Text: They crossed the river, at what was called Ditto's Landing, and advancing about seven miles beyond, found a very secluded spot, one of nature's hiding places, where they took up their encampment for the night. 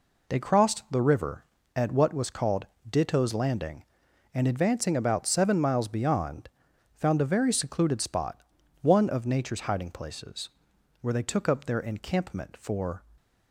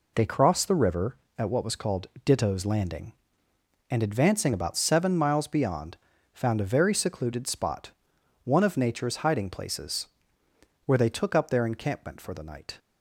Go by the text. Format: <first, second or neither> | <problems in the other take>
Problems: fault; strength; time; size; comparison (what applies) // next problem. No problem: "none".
second | pauses between "called" and "Ditto's"; slight; at 2.6 s; 0.22 s long; slight in the second // stops before "the night"; at 13.1 s